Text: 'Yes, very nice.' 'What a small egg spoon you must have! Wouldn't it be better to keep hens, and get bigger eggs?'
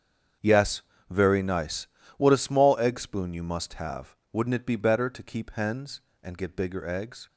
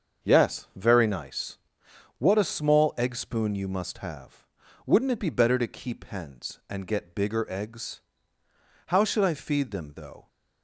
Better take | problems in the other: first | starts louder than the rest; until 1.3 s; 7 dB; strong in the first // goes on to say "How should I feed them though"; from 8.8 s on; 1.4 s long

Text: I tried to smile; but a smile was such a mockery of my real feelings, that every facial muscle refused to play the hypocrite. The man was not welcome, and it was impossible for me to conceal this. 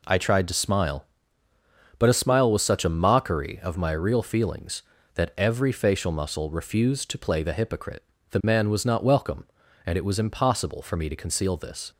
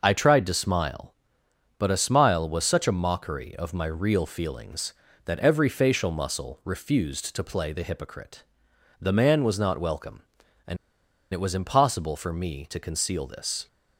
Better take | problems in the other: first | pauses between "and" and "it"; noticeable; at 10.7 s; 0.56 s long

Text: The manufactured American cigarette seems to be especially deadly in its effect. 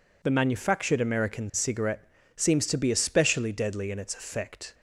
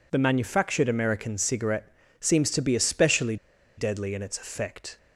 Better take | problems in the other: first | pauses between "cigarette" and "seems"; slight; at 1.9 s; 0.26 s long; slight in the first // pauses between "especially" and "deadly"; at 3.3 s; 0.41 s long

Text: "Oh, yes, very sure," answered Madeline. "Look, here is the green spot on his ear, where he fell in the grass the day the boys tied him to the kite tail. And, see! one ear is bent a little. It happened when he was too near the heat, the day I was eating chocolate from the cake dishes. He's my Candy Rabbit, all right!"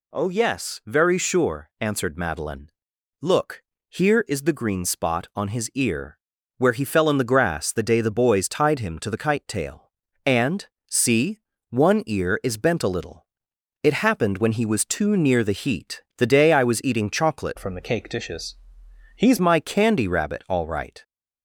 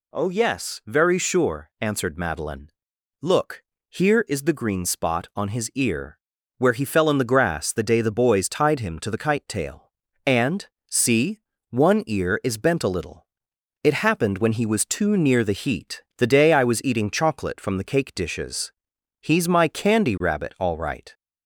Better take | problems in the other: second | changes voice from "from" to "He's"; from 17.5 to 19.3 s; 1.8 s long

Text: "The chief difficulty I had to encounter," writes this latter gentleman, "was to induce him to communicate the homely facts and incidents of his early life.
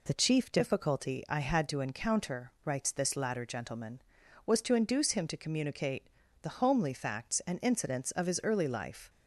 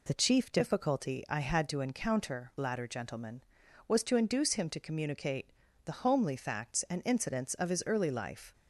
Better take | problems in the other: first | skips "writes this"; at 2.5 s // pauses between "communicate" and "the"; at 5.4 s; 0.38 s long; also in the first

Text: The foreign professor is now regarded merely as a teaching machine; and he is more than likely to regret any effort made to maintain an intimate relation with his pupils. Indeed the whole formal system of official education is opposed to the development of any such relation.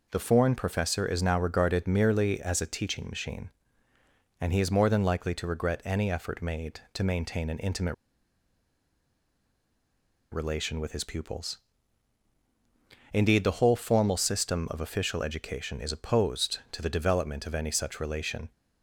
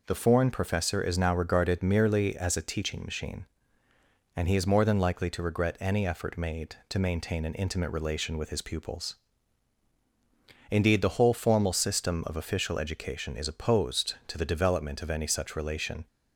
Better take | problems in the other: second | pauses between "intimate" and "relation"; strong; at 7.9 s; 2.3 s long

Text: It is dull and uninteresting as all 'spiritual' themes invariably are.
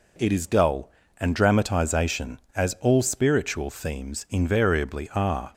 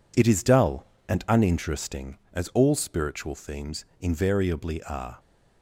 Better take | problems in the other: second | says "dramatization" for "uninteresting"; at 1.3 s

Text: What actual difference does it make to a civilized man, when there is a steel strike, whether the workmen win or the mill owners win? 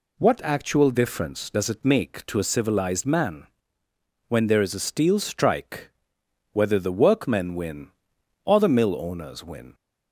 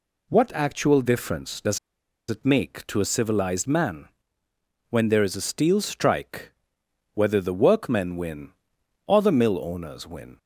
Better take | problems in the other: first | pauses between "does" and "it"; noticeable; at 1.7 s; 0.51 s long

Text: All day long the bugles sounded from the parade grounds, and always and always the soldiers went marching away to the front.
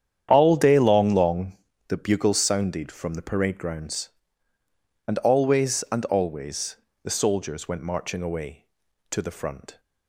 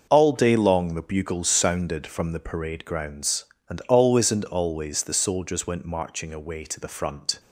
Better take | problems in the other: second | starts louder than the rest; strong; until 1.3 s; 9.5 dB // says "long" twice; at 1.1 s // pauses between "always" and "the"; slight; at 6.7 s; 0.26 s long

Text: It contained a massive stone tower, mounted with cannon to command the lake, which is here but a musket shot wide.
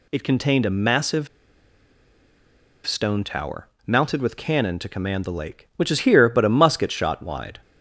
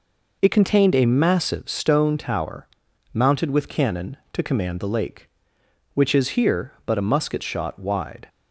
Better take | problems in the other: second | pauses between "massive" and "stone"; strong; at 1.2 s; 1.5 s long

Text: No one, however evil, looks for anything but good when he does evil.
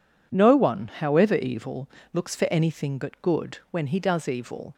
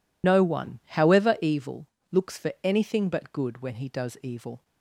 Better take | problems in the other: first | loses the start of "No"; at 0.2 s; 75 ms

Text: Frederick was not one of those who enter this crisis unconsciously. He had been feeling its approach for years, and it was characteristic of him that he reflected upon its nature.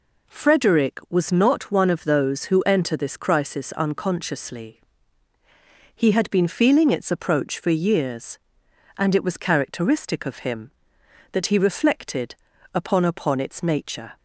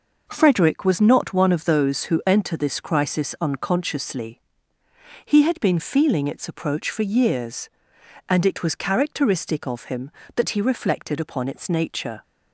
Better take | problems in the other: second | pauses between "reflected" and "upon"; at 12.3 s; 0.40 s long // says "upon" twice; at 13.0 s

